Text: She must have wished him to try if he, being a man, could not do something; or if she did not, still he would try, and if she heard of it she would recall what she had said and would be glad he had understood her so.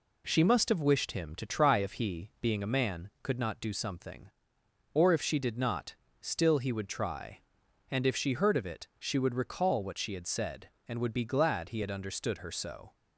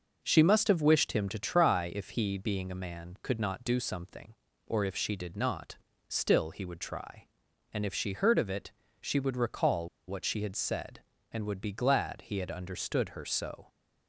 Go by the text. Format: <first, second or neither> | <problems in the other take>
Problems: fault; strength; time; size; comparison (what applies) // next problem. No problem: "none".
first | pauses between "it" and "she"; slight; at 8.7 s; 0.30 s long // pauses between "recall" and "what"; slight; at 9.8 s; 0.19 s long